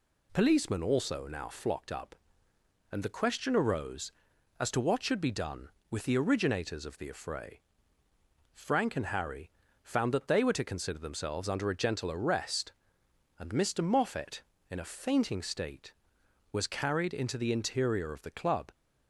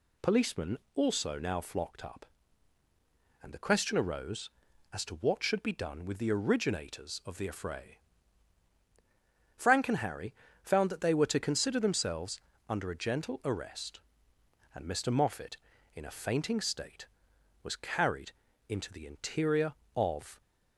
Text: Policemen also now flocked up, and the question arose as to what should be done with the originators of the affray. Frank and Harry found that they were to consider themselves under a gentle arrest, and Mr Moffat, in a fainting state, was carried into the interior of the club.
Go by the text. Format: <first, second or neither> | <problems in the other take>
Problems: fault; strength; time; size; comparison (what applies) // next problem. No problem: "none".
first | pauses between "Policemen" and "also"; slight; at 0.7 s; 0.18 s long // pauses between "Harry" and "found"; slight; at 10.3 s; 0.26 s long; slight in the first // pauses between "themselves" and "under"; slight; at 12.4 s; 0.28 s long // pauses between "carried" and "into"; slight; at 18.3 s; 0.34 s long // stops before "the club"; at 20.4 s